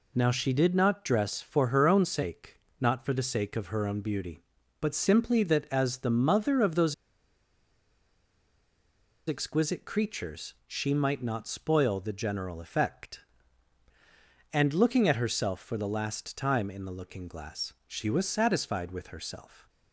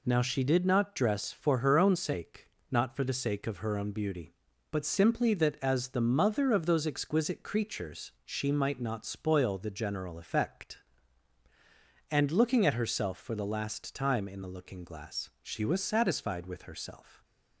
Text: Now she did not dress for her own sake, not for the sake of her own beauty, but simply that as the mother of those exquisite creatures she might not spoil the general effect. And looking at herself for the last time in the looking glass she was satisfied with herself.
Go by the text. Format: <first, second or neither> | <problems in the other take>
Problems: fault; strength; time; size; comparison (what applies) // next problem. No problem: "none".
second | pauses between "those" and "exquisite"; strong; at 6.9 s; 2.3 s long // pauses between "creatures" and "she"; slight; at 10.5 s; 0.16 s long; slight in the second // pauses between "glass" and "she"; slight; at 17.7 s; 0.16 s long